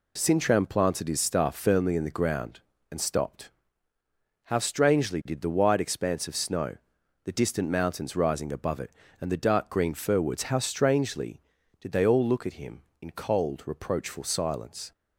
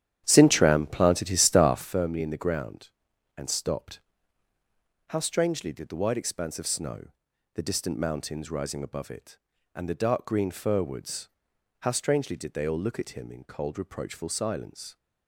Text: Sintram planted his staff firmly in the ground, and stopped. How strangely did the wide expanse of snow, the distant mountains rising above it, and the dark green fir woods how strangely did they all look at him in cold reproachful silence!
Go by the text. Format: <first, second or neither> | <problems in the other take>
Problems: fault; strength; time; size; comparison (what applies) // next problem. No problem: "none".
first | starts louder than the rest; strong; until 1.9 s; 10.5 dB // pauses between "woods" and "how"; noticeable; at 11.2 s; 0.56 s long